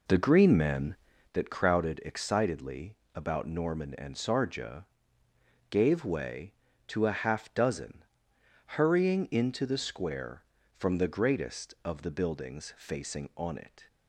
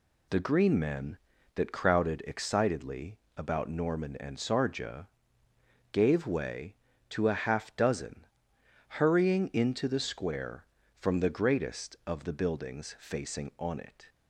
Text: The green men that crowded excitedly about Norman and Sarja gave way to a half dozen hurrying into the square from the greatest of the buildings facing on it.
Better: second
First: starts louder than the rest; noticeable; until 1.3 s; 4 dB // pauses between "excitedly" and "about"; slight; at 2.9 s; 0.20 s long // pauses between "Sarja" and "gave"; noticeable; at 4.8 s; 0.86 s long // pauses between "dozen" and "hurrying"; noticeable; at 8.0 s; 0.62 s long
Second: pauses between "excitedly" and "about"; slight; at 3.1 s; 0.20 s long // pauses between "Sarja" and "gave"; noticeable; at 5.0 s; 0.86 s long // pauses between "dozen" and "hurrying"; noticeable; at 8.2 s; 0.62 s long

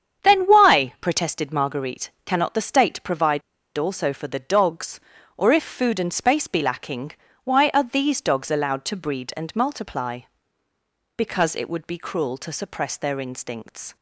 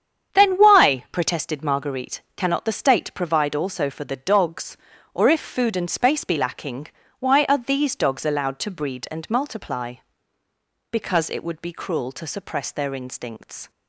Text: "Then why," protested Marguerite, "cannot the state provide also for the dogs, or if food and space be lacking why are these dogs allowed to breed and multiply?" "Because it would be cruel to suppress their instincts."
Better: second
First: starts louder than the rest; strong; until 1.3 s; 8 dB // pauses between "provide" and "also"; slight; at 3.4 s; 0.34 s long // pauses between "lacking" and "why"; slight; at 7.1 s; 0.32 s long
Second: starts louder than the rest; strong; until 1.4 s; 8 dB // pauses between "lacking" and "why"; slight; at 6.8 s; 0.32 s long

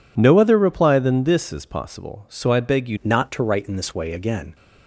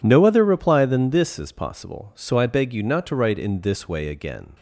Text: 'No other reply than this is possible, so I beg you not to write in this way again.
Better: second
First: changes voice at "not"; from 3.0 s on; 1.5 s long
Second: none

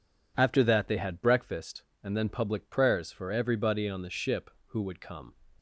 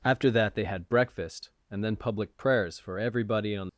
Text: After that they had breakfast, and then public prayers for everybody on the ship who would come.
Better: first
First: none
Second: stops before "the ship who would come"; at 3.6 s

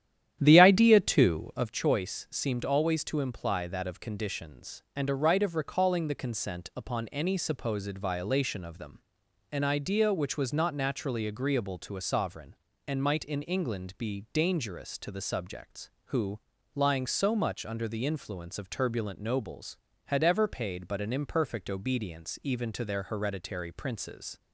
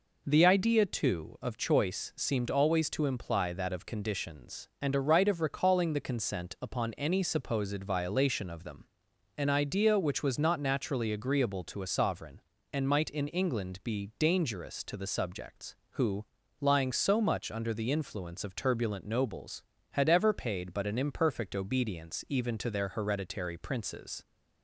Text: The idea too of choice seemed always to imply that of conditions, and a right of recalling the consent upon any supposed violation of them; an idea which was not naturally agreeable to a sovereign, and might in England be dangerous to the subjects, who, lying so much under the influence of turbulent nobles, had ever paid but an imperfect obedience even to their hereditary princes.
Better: second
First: starts louder than the rest; strong; until 1.8 s; 11 dB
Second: none

